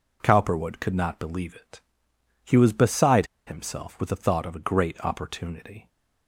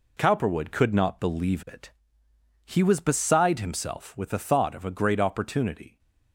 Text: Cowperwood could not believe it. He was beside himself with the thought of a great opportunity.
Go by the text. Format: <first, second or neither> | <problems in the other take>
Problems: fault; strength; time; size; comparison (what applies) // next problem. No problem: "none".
second | pauses between "beside" and "himself"; slight; at 3.2 s; 0.20 s long